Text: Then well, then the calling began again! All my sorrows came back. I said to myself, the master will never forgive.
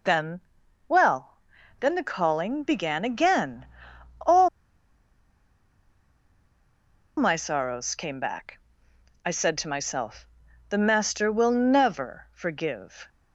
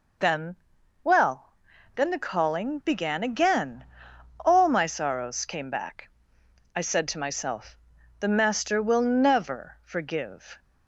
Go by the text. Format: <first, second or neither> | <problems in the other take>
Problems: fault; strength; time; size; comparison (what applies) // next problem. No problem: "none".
second | pauses between "Then" and "well"; noticeable; at 0.3 s; 0.48 s long; noticeable in the second // pauses between "All" and "my"; strong; at 4.4 s; 2.6 s long